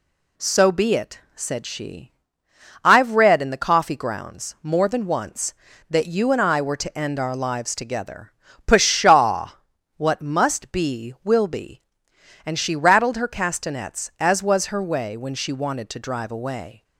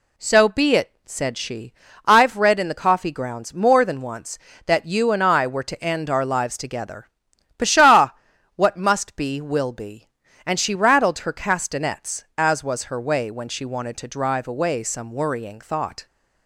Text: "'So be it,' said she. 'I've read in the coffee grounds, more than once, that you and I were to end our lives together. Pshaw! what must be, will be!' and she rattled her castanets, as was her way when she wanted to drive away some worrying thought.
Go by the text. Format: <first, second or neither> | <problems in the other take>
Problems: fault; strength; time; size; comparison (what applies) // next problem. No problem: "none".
second | stops before "some worrying thought"; at 16.8 s